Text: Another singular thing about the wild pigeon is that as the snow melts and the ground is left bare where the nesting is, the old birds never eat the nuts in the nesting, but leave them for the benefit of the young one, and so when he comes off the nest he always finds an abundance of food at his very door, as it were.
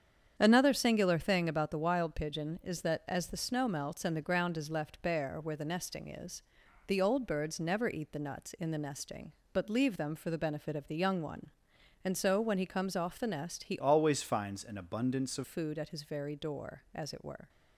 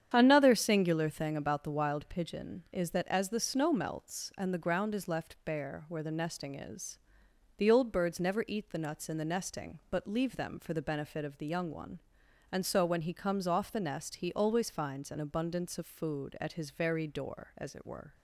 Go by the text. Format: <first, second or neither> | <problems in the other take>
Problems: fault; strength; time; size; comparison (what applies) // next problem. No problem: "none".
second | starts louder than the rest; strong; until 1.3 s; 8 dB; strong in the second // changes voice from "always" to "of"; from 13.7 to 15.4 s; 1.7 s long